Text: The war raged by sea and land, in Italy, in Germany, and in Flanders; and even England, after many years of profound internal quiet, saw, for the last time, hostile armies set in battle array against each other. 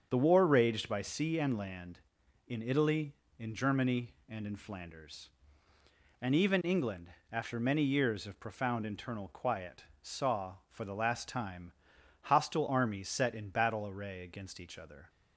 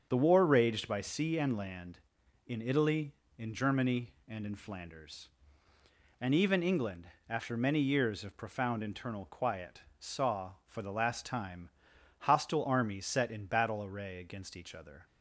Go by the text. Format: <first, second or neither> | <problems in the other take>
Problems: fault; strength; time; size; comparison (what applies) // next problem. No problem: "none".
neither | starts louder than the rest; the same in both